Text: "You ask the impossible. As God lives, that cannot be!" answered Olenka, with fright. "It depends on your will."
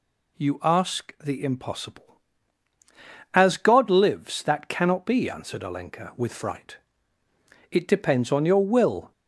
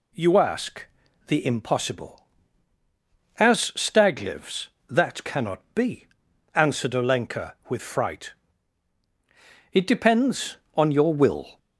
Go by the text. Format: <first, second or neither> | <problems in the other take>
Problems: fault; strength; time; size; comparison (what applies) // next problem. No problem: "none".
first | pauses between "ask" and "the"; at 0.8 s; 0.42 s long // says "Stag" for "God"; at 3.7 s